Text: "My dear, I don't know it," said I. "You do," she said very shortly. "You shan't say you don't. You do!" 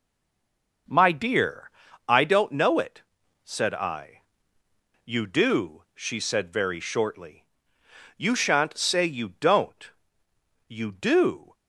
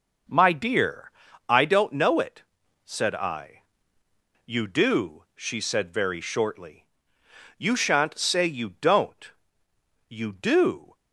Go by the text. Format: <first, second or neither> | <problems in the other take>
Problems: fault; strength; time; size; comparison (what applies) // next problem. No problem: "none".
second | stays silent before the first word; slight; until 0.8 s; 0.8 s long